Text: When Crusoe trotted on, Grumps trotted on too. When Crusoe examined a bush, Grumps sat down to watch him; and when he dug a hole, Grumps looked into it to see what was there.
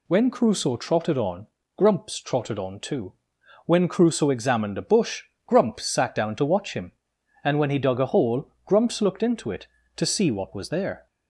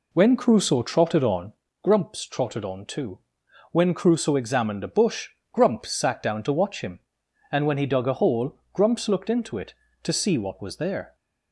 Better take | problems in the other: first | starts louder than the rest; slight; until 1.7 s; 3 dB

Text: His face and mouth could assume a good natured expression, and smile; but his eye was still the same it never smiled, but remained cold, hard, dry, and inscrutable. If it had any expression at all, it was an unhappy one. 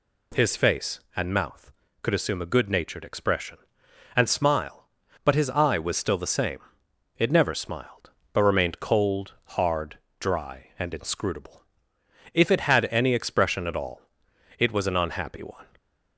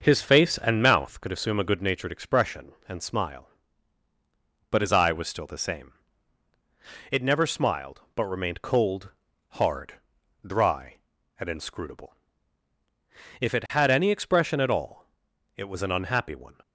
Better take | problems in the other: first | starts louder than the rest; until 1.2 s; 6.5 dB // pauses between "same" and "it"; at 5.9 s; 1.2 s long; noticeable in the first

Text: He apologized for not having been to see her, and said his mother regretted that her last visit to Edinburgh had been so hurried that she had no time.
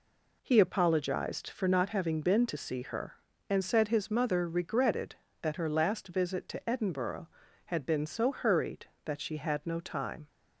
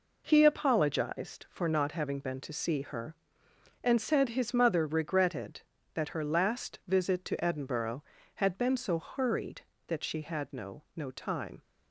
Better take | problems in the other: first | says "no" twice; at 10.9 s

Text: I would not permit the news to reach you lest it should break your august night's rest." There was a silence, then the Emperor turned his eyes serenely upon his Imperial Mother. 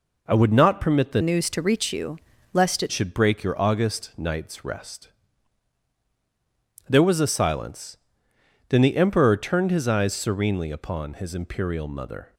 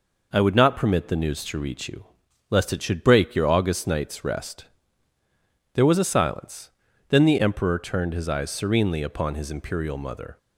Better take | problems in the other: second | changes voice from "news" to "it"; from 1.2 to 2.9 s; 1.7 s long // pauses between "you" and "lest"; slight; at 2.1 s; 0.36 s long; also in the second

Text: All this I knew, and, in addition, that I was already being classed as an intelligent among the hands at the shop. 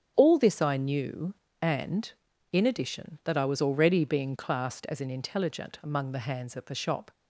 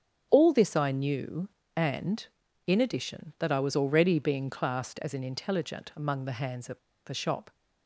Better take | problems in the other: first | starts louder than the rest; strong; until 1.3 s; 8.5 dB; strong in the first // pauses between "at" and "the"; slight; at 6.7 s; 0.27 s long

